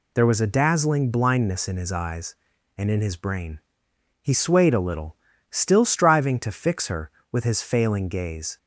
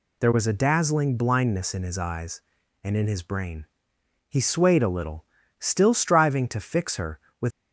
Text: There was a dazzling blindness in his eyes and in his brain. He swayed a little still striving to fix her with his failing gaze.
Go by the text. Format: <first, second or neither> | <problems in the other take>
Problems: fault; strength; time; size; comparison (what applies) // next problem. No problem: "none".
first | pauses between "little" and "still"; slight; at 5.2 s; 0.36 s long; slight in the first // stops before "his failing gaze"; at 7.5 s